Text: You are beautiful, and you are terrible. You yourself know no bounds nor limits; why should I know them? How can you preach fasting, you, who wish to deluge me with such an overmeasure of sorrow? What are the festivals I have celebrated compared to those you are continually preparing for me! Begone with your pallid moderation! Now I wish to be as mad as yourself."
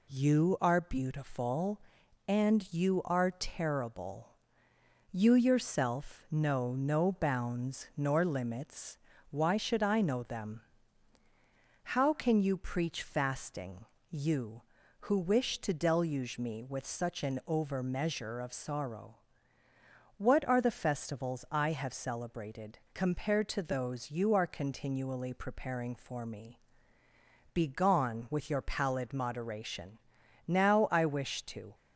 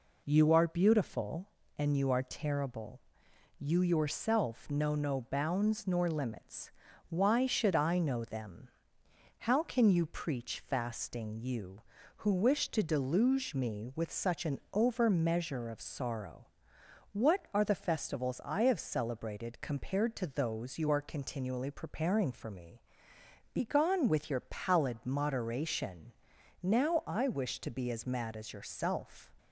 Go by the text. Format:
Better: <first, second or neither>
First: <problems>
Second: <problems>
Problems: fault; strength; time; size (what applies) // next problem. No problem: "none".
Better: second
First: stops before "be as mad as yourself"; at 31.7 s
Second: none